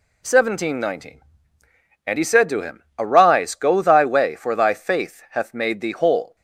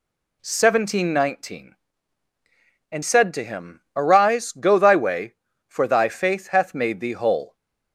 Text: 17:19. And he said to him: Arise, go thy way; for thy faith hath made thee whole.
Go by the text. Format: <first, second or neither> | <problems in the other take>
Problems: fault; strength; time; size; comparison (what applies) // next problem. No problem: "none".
first | skips "he"; at 3.0 s